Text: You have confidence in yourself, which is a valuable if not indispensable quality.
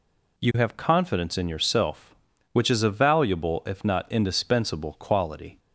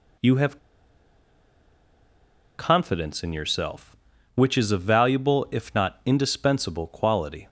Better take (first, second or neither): first